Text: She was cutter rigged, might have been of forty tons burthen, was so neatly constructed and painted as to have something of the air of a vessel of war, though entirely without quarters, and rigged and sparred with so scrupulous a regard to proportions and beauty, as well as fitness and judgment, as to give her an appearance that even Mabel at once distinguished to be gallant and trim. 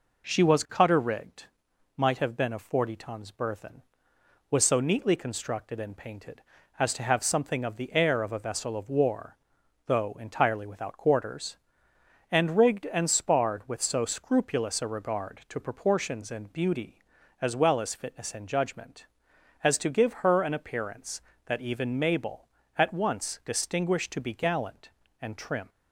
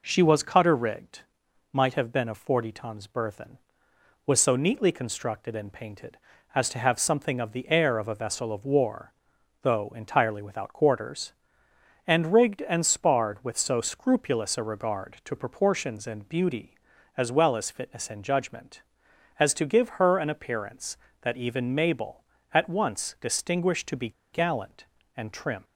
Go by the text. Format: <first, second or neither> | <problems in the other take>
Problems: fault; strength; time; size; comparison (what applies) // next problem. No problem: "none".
first | pauses between "be" and "gallant"; slight; at 24.1 s; 0.22 s long